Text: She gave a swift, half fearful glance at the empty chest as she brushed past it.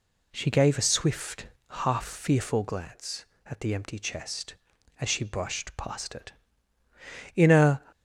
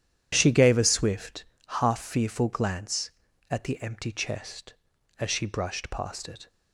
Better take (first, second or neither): second